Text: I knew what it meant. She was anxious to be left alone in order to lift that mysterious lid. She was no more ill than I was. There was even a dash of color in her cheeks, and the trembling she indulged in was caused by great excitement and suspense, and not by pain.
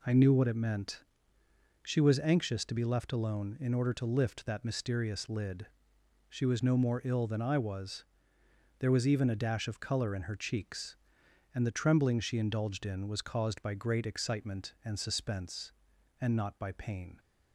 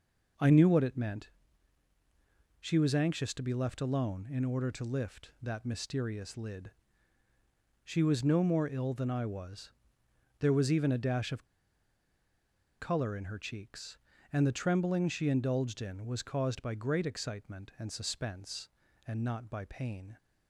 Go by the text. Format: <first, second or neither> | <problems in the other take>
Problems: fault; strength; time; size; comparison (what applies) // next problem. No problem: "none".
first | pauses between "of" and "color"; strong; at 11.4 s; 1.3 s long